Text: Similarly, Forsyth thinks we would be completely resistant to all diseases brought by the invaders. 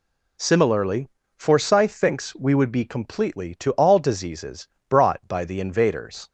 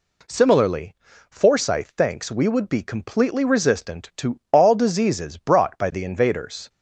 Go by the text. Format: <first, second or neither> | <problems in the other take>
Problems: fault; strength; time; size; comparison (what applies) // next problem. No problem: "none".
second | skips "resistant"; at 3.5 s // pauses between "diseases" and "brought"; slight; at 4.6 s; 0.22 s long